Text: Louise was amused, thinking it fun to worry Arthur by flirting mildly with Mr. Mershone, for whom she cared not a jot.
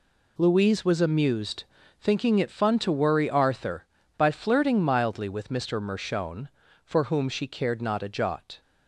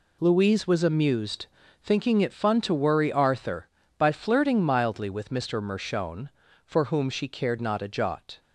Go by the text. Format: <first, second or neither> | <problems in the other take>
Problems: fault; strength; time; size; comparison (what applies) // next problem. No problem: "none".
neither | none